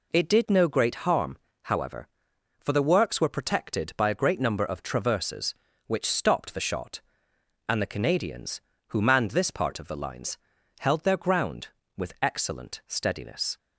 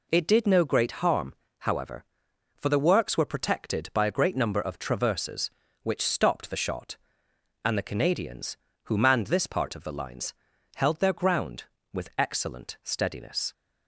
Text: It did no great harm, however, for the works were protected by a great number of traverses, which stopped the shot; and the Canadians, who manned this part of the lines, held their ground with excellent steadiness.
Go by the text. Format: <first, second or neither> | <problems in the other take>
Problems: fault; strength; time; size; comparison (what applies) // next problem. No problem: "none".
neither | none